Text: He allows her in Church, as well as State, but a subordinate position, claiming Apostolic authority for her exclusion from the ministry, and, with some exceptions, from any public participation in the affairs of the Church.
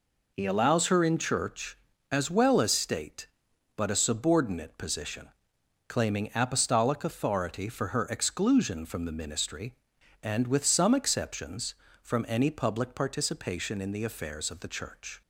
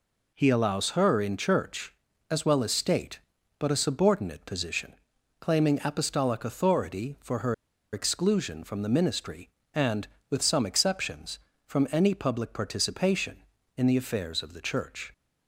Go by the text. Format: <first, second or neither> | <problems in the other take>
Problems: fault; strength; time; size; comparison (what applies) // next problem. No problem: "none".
first | pauses between "her" and "exclusion"; at 7.5 s; 0.38 s long